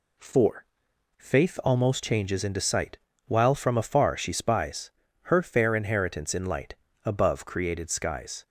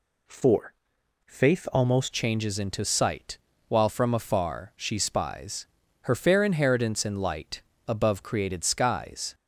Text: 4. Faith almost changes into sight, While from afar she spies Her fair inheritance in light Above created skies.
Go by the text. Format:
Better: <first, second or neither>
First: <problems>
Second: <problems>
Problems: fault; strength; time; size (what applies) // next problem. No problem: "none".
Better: first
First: pauses between "spies" and "Her"; slight; at 4.9 s; 0.30 s long // pauses between "light" and "Above"; slight; at 6.7 s; 0.28 s long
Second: changes voice at "changes"; from 2.1 s on; 7.2 s long // pauses between "spies" and "Her"; slight; at 5.6 s; 0.36 s long // pauses between "light" and "Above"; slight; at 7.6 s; 0.26 s long